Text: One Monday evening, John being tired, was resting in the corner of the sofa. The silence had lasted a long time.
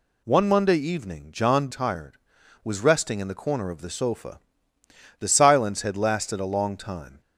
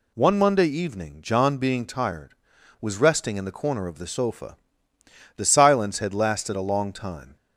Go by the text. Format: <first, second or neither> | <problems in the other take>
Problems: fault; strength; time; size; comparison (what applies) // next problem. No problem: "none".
second | skips "being"; at 1.6 s